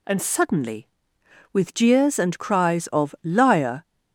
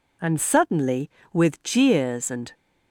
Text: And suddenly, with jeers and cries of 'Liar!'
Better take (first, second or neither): first